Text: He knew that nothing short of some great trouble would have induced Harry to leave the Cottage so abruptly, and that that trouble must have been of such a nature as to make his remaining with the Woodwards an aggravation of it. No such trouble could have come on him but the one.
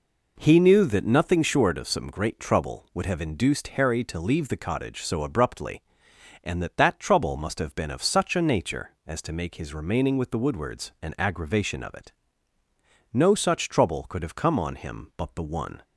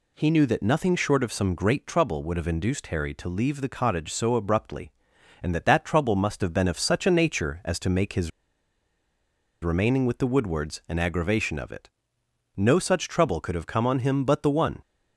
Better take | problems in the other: first | pauses between "his" and "remaining"; strong; at 8.3 s; 1.3 s long

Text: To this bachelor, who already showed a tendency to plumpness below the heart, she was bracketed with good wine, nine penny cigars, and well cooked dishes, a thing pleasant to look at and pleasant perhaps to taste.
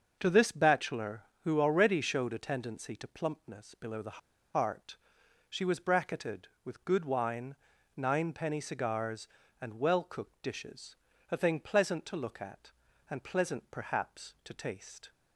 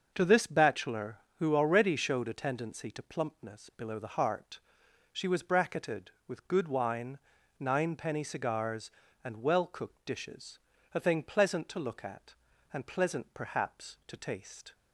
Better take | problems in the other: second | starts louder than the rest; until 1.2 s; 6.5 dB; also in the second // pauses between "the" and "heart"; slight; at 4.1 s; 0.36 s long

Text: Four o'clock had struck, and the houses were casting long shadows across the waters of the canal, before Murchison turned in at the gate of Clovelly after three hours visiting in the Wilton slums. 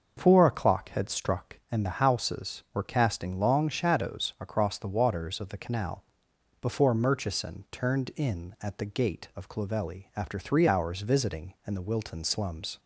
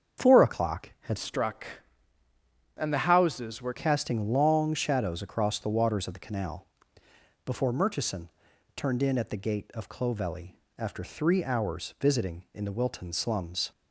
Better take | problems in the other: first | starts louder than the rest; strong; until 1.3 s; 7.5 dB // changes voice from "struck" to "were"; from 1.1 to 3.7 s; 2.6 s long // pauses between "Murchison" and "turned"; at 8.3 s; 0.44 s long // pauses between "Clovelly" and "after"; slight; at 10.5 s; 0.24 s long

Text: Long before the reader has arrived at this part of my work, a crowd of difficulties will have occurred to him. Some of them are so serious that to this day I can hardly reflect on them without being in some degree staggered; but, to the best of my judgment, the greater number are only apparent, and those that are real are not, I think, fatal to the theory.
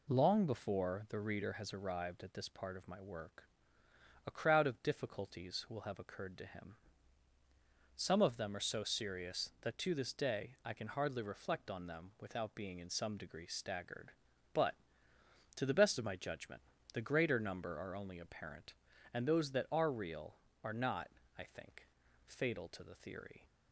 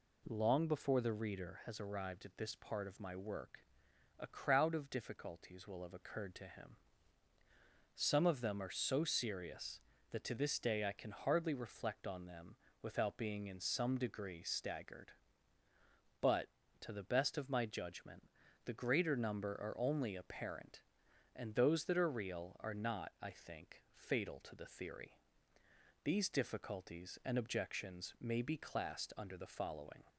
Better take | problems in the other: first | pauses between "them" and "without"; slight; at 12.5 s; 0.26 s long // goes on to say "These difficulties and objections may be classed under the following"; strong; from 26.0 s on; 4.0 s long

